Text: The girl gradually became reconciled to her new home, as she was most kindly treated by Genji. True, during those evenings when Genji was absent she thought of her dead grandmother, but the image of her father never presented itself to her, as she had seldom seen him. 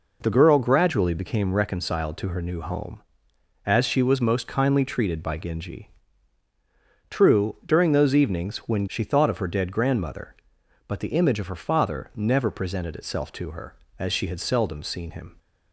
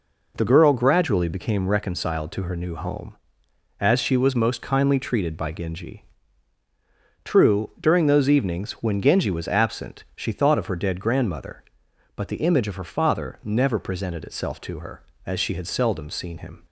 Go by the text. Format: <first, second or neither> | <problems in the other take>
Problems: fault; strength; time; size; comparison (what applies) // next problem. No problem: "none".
second | skips "Genji was absent"; at 8.8 s